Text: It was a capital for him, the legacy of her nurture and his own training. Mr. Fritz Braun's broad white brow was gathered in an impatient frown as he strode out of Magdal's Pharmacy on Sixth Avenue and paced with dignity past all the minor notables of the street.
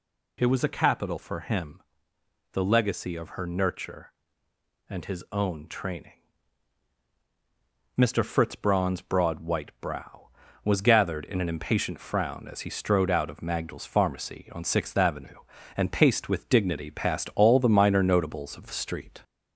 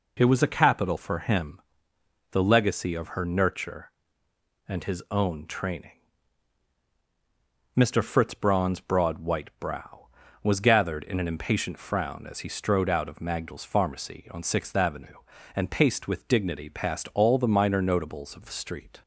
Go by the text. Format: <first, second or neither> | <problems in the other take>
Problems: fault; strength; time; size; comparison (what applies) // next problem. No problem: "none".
second | gets louder; slight; throughout; 2 dB